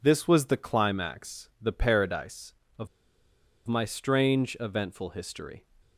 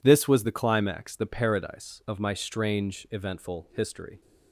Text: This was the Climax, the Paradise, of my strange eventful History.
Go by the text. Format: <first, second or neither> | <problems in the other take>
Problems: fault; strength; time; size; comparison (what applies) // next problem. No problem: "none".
second | pauses between "of" and "my"; noticeable; at 2.8 s; 0.79 s long